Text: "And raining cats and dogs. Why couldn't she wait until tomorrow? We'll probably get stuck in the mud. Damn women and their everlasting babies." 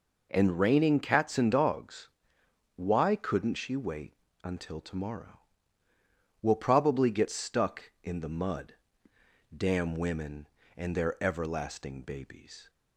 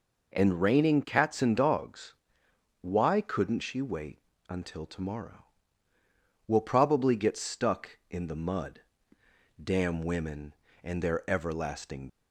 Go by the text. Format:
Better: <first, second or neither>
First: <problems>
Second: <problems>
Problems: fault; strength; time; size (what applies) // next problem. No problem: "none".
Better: first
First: pauses between "wait" and "until"; slight; at 4.1 s; 0.30 s long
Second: pauses between "wait" and "until"; slight; at 4.1 s; 0.30 s long // stops before "babies"; at 12.0 s